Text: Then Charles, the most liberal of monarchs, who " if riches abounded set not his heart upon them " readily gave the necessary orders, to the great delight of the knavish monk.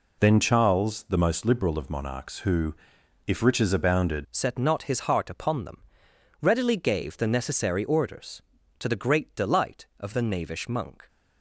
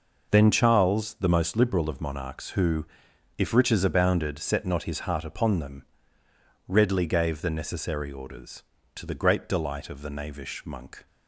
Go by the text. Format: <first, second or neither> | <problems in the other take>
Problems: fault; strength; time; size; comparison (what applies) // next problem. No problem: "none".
second | changes voice at "set"; from 4.3 s on; 6.7 s long